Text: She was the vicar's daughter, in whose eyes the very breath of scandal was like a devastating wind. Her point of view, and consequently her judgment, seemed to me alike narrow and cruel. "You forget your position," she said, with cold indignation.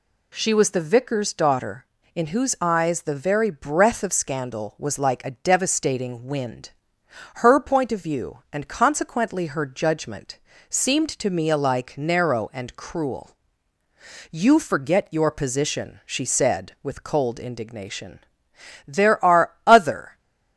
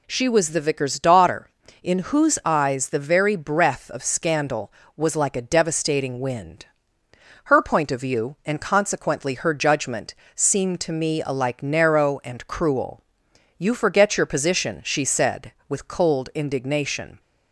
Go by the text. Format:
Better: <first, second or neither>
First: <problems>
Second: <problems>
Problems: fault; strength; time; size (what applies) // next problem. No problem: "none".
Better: second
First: goes on to say "There are other"; noticeable; from 18.8 s on; 1.3 s long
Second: none